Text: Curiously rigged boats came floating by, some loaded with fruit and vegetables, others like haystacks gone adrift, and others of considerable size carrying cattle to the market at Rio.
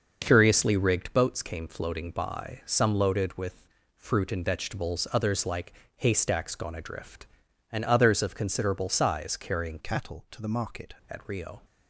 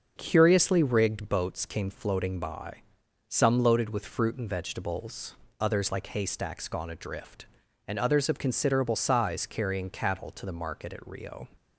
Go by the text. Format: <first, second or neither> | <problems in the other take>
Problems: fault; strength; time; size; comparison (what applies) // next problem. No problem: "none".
second | starts louder than the rest; noticeable; until 1.2 s; 6 dB; also in the second // pauses between "with" and "fruit"; slight; at 3.6 s; 0.32 s long // pauses between "like" and "haystacks"; slight; at 5.7 s; 0.24 s long // changes voice from "cattle" to "market"; from 9.8 to 10.9 s; 1.1 s long